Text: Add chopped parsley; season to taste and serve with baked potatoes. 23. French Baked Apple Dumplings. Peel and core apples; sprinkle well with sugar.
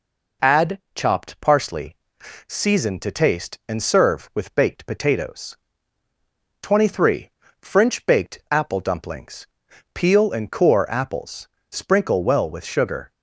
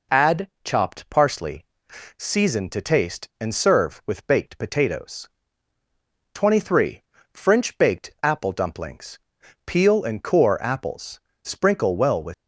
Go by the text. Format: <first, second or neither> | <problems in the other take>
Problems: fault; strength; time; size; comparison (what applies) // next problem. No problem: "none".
first | stops before "sugar"; at 12.3 s